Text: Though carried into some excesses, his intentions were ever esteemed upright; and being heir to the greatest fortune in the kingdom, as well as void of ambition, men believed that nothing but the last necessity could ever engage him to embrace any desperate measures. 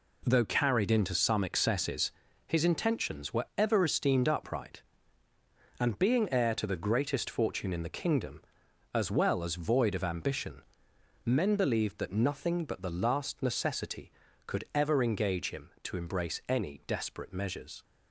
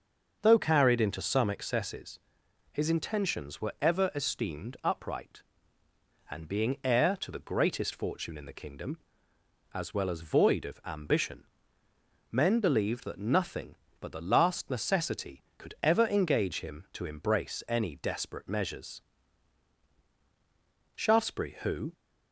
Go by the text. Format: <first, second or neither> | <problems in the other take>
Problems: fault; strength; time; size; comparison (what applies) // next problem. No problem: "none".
first | starts louder than the rest; until 1.4 s; 6.5 dB // goes on to say "Shaftesbury who"; noticeable; from 20.9 s on; 0.98 s long